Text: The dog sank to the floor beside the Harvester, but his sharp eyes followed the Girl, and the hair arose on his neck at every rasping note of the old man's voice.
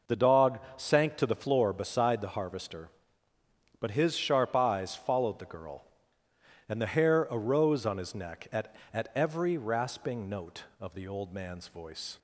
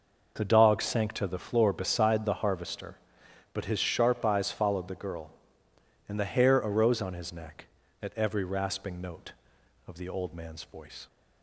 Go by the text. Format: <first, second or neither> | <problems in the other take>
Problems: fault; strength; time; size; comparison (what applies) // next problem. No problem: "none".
second | pauses between "dog" and "sank"; slight; at 0.5 s; 0.16 s long // says "at" twice; at 8.9 s